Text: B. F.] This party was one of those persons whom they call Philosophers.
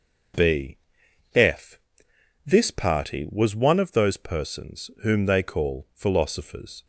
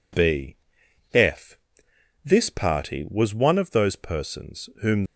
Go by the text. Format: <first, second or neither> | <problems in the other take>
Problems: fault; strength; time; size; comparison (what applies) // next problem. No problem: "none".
first | pauses between "B" and "F"; noticeable; at 0.5 s; 0.54 s long; noticeable in the first // pauses between "F" and "This"; noticeable; at 1.5 s; 0.66 s long; noticeable in the first // stops before "they call Philosophers"; at 5.0 s